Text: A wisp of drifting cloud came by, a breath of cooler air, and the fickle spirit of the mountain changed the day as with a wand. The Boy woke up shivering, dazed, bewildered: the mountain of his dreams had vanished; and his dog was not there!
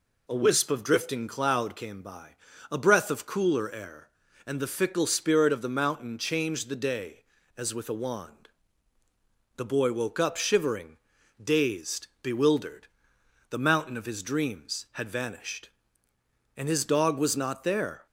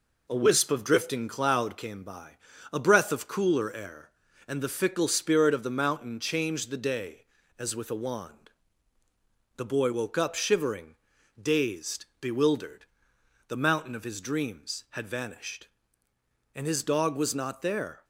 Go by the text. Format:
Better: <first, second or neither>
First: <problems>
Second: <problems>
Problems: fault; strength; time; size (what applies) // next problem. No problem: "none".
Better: first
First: none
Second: gets quieter; noticeable; throughout; 4.5 dB